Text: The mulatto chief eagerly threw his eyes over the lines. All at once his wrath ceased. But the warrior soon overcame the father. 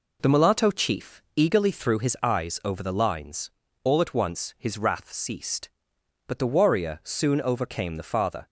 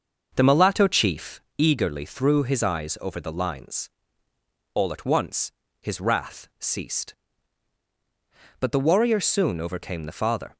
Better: first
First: none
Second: starts louder than the rest; until 1.5 s; 6 dB // pauses between "chief" and "eagerly"; slight; at 1.4 s; 0.18 s long // pauses between "once" and "his"; slight; at 5.5 s; 0.28 s long

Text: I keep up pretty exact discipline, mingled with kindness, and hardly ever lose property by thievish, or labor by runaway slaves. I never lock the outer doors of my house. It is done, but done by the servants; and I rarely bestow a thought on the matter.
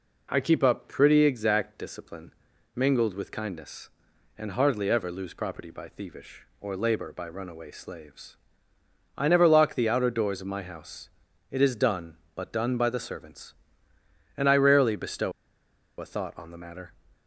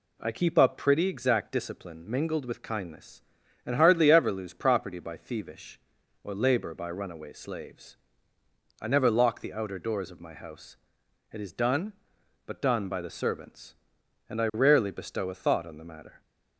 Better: second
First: pauses between "bestow" and "a"; noticeable; at 15.3 s; 0.67 s long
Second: none

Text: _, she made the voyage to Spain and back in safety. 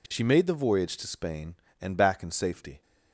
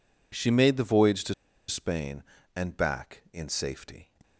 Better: first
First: none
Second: pauses between "to" and "Spain"; slight; at 1.3 s; 0.35 s long

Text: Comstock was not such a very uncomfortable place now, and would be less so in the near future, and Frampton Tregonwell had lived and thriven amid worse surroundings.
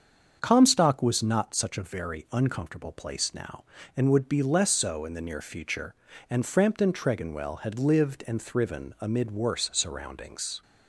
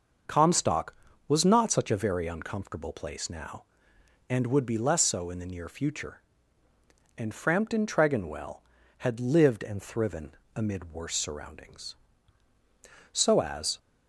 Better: first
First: starts louder than the rest; until 1.4 s; 7 dB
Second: starts louder than the rest; until 1.6 s; 6.5 dB // pauses between "thriven" and "amid"; slight; at 10.3 s; 0.22 s long // goes on to say "So as"; noticeable; from 13.1 s on; 0.66 s long

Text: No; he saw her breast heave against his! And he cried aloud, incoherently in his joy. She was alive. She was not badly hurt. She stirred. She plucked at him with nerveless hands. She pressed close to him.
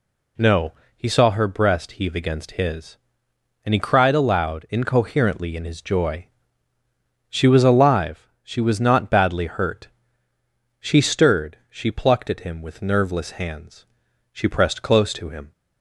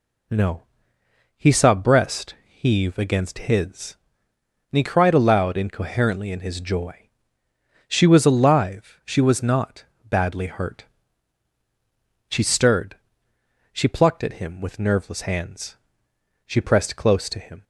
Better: first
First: none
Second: skips "her"; at 1.7 s // pauses between "not" and "badly"; slight; at 9.8 s; 0.20 s long

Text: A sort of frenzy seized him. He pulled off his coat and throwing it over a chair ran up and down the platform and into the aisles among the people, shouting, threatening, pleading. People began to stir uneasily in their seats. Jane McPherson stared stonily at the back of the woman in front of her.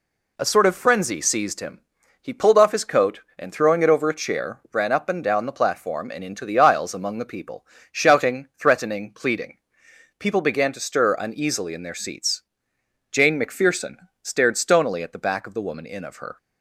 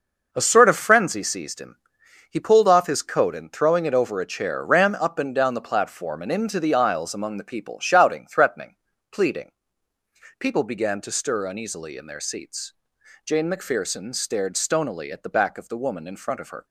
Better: second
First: pauses between "McPherson" and "stared"; slight; at 13.9 s; 0.28 s long // skips "front"; at 16.0 s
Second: none

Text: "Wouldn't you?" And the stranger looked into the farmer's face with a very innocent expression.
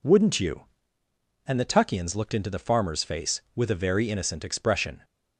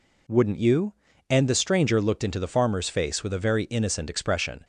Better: second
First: says "tuckians" for "stranger"; at 1.6 s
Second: none

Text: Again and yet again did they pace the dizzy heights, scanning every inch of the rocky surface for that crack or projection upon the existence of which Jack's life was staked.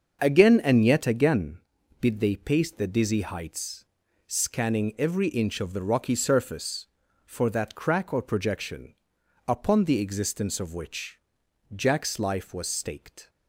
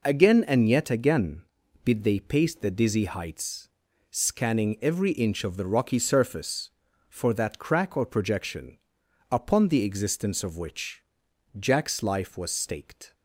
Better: second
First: starts louder than the rest; until 1.4 s; 7 dB // pauses between "projection" and "upon"; noticeable; at 8.9 s; 0.52 s long // pauses between "which" and "Jack's"; noticeable; at 11.1 s; 0.54 s long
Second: pauses between "projection" and "upon"; noticeable; at 8.7 s; 0.52 s long // pauses between "which" and "Jack's"; noticeable; at 11.0 s; 0.54 s long

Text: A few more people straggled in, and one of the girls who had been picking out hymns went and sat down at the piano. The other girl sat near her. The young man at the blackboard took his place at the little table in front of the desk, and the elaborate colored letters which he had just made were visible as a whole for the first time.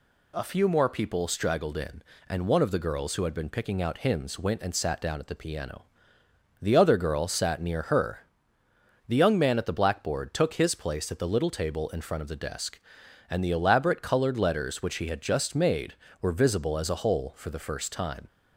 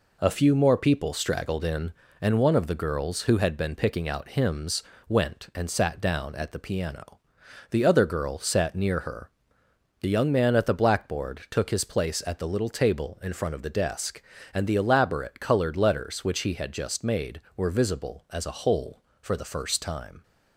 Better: first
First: none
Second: gets quieter; noticeable; throughout; 5 dB // pauses between "hymns" and "went"; slight; at 4.8 s; 0.24 s long

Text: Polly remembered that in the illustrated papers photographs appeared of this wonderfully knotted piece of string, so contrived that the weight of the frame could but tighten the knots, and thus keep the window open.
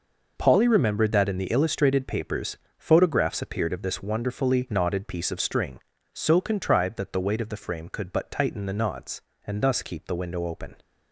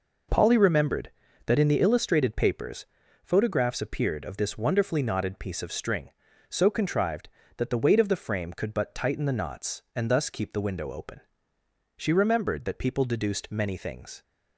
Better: first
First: pauses between "papers" and "photographs"; slight; at 2.5 s; 0.20 s long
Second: pauses between "papers" and "photographs"; at 2.8 s; 0.38 s long // goes on to say "She remembered that people deduced many things"; strong; from 11.9 s on; 2.2 s long

